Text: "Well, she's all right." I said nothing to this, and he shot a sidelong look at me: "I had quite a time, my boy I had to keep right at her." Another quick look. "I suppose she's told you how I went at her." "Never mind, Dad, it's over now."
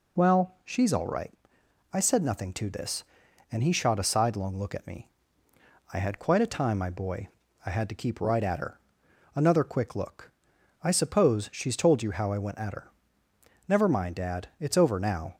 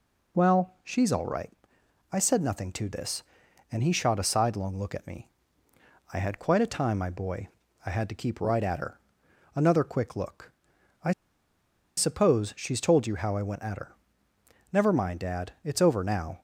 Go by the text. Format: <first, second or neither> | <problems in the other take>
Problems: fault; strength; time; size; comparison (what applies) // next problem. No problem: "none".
first | pauses between "boy" and "I"; at 7.4 s; 0.38 s long; also in the first // pauses between "I" and "suppose"; noticeable; at 11.1 s; 0.85 s long